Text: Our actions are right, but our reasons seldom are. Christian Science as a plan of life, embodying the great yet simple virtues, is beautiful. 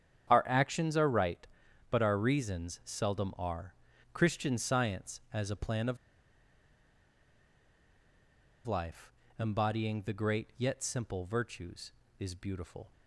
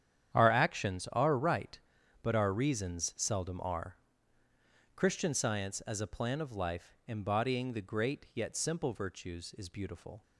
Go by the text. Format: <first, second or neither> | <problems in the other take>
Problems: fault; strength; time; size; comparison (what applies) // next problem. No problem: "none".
second | starts louder than the rest; strong; until 1.3 s; 9 dB; strong in the second // pauses between "of" and "life"; strong; at 5.9 s; 2.7 s long